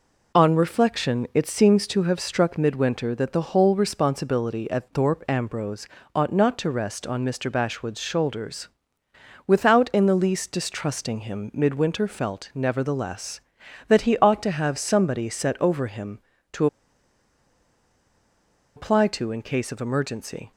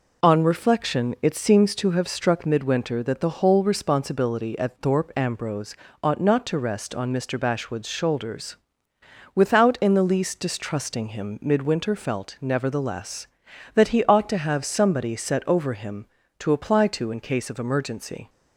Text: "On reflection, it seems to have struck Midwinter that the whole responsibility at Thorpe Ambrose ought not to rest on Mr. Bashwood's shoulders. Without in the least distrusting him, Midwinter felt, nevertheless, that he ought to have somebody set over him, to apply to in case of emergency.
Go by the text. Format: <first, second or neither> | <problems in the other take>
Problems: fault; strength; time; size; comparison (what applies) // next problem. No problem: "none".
second | pauses between "Ambrose" and "ought"; slight; at 5.8 s; 0.28 s long; slight in the second // pauses between "to" and "apply"; strong; at 16.6 s; 2.0 s long